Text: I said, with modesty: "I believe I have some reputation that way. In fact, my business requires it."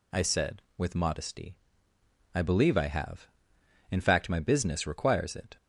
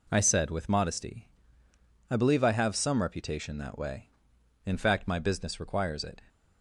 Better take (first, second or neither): second